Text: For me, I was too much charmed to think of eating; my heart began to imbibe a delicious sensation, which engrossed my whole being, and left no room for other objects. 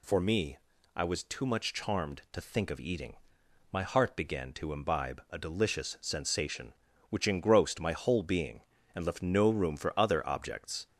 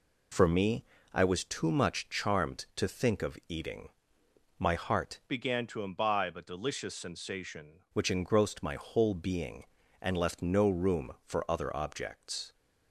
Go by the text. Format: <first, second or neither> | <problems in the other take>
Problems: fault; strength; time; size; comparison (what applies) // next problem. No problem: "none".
first | changes voice from "began" to "sensation"; from 5.2 to 7.7 s; 2.5 s long